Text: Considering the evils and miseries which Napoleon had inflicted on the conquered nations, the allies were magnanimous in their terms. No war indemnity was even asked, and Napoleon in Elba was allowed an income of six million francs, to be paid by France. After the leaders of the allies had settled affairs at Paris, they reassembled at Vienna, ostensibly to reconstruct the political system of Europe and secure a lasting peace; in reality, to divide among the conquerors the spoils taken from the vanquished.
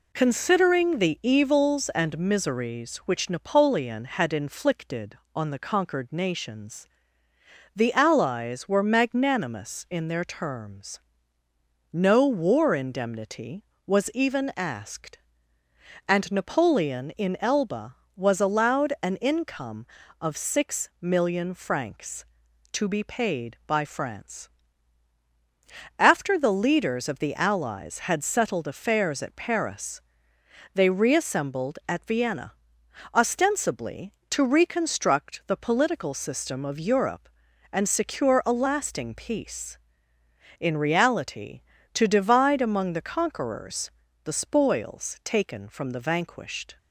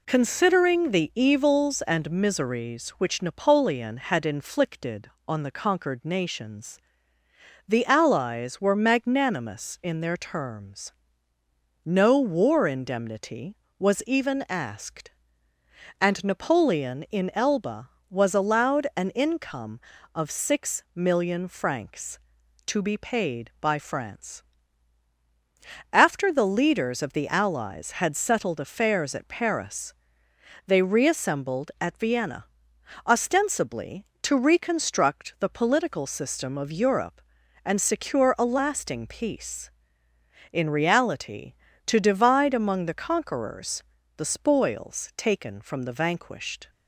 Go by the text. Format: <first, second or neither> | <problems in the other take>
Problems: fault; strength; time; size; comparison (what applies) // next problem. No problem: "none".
neither | pauses between "conquerors" and "the"; slight; the same in both